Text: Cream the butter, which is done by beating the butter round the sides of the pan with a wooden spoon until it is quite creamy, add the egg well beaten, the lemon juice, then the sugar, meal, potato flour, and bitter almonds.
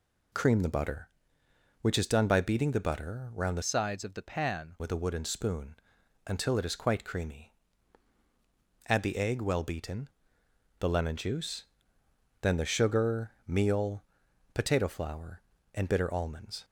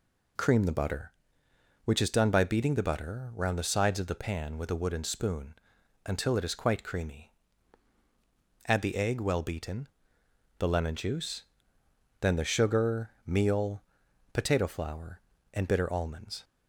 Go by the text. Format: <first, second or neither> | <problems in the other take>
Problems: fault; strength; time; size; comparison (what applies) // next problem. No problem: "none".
second | changes voice from "sides" to "pan"; from 3.6 to 4.7 s; 1.1 s long // pauses between "spoon" and "until"; noticeable; at 5.7 s; 0.52 s long; noticeable in the second